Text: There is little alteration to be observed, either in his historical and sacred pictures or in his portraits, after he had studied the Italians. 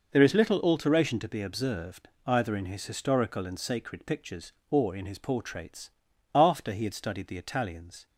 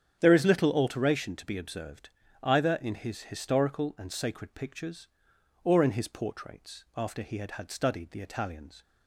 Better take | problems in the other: first | starts louder than the rest; strong; until 1.2 s; 8.5 dB // says "had" twice; at 7.5 s

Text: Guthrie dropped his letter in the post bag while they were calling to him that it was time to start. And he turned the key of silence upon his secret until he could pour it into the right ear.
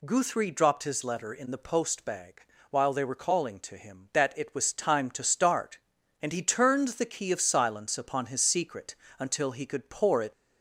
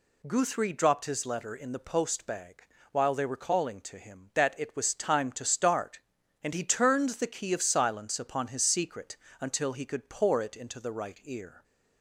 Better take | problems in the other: second | pauses between "bag" and "while"; slight; at 2.4 s; 0.28 s long; slight in the second // pauses between "secret" and "until"; slight; at 8.9 s; 0.24 s long; slight in the second // stops before "into the right ear"; at 10.3 s

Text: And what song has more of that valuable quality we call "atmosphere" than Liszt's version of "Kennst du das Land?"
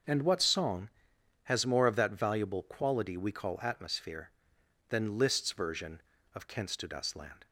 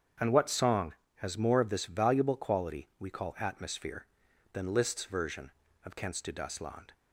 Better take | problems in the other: first | starts louder than the rest; strong; until 1.4 s; 8 dB; also in the first // says "this" for "that"; at 1.6 s

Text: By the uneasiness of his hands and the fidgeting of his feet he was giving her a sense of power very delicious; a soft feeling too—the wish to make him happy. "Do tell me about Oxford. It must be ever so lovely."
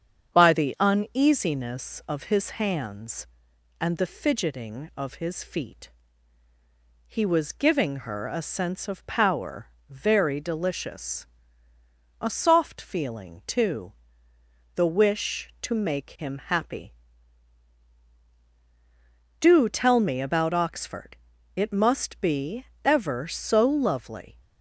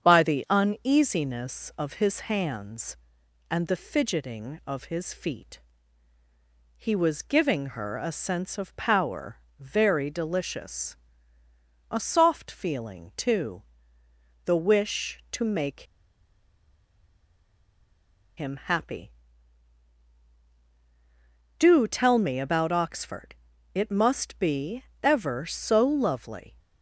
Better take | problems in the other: first | starts louder than the rest; strong; until 1.0 s; 7.5 dB; strong in the first // pauses between "feet" and "he"; at 5.6 s; 1.1 s long; also in the first // pauses between "power" and "very"; slight; at 9.3 s; 0.24 s long; slight in the first // pauses between "make" and "him"; strong; at 15.8 s; 2.5 s long // pauses between "be" and "ever"; slight; at 24.8 s; 0.18 s long; slight in the first

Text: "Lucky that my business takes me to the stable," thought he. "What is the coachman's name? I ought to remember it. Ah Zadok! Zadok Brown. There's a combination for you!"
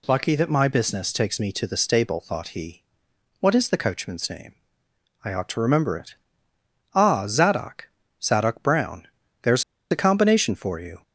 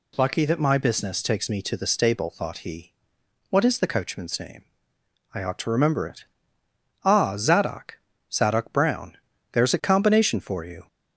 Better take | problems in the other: second | pauses between "There's" and "a"; slight; at 9.6 s; 0.28 s long

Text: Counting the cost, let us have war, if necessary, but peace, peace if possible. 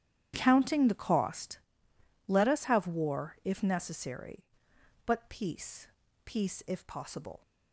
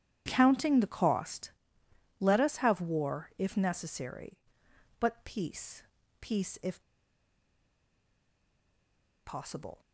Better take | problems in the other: first | starts louder than the rest; strong; until 1.2 s; 10.5 dB; strong in the first // pauses between "if" and "possible"; strong; at 6.8 s; 2.4 s long

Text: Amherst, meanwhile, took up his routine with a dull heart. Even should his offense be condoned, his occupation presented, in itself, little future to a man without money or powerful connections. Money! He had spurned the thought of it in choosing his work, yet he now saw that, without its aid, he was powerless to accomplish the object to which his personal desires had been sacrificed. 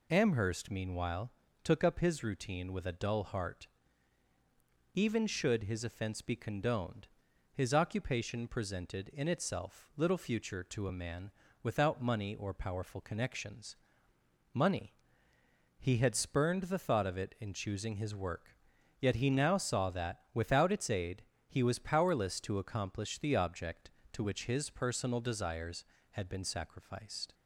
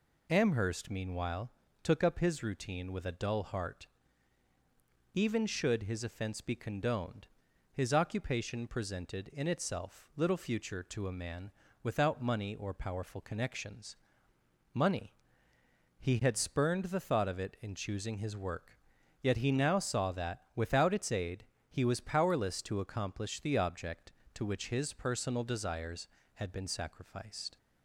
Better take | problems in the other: neither | pauses between "man" and "without"; slight; the same in both

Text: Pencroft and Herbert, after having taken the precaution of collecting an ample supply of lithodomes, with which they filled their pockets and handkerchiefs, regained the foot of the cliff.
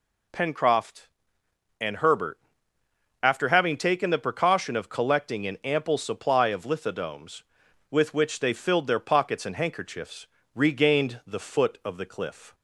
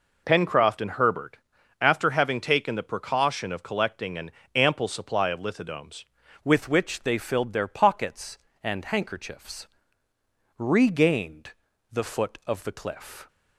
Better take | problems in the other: first | pauses between "an" and "ample"; slight; at 4.3 s; 0.24 s long // changes voice at "with"; from 6.4 s on; 6.8 s long // pauses between "regained" and "the"; at 11.5 s; 0.40 s long

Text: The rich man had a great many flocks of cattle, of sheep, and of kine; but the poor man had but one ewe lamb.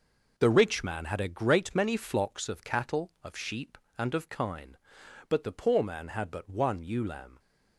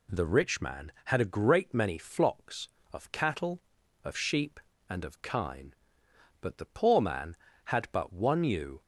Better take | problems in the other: first | stops before "lamb"; at 8.8 s

